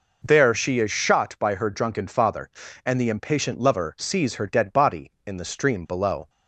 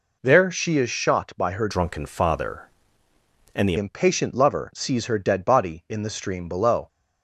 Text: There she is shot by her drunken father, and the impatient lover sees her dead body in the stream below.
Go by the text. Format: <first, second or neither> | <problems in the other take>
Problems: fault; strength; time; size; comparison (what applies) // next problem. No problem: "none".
first | changes voice from "drunken" to "the"; from 1.6 to 3.7 s; 2.1 s long